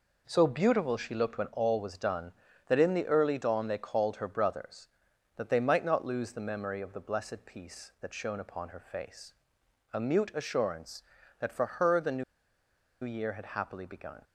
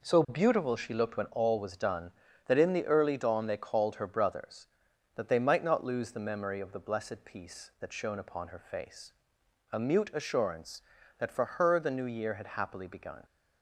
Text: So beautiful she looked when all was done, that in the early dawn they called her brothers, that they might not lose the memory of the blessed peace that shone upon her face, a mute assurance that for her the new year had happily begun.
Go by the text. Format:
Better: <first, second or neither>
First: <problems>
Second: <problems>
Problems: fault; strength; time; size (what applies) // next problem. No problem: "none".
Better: second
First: pauses between "new" and "year"; noticeable; at 12.2 s; 0.79 s long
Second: none